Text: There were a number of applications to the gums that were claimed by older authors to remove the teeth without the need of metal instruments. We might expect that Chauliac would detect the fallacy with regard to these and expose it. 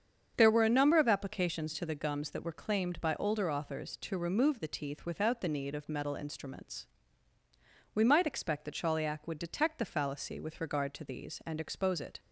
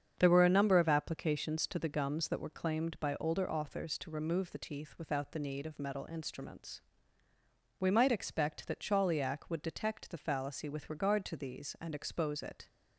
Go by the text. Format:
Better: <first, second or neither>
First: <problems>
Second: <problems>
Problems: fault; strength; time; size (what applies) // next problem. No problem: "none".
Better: neither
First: starts louder than the rest; strong; until 1.3 s; 7.5 dB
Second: starts louder than the rest; strong; until 1.1 s; 7.5 dB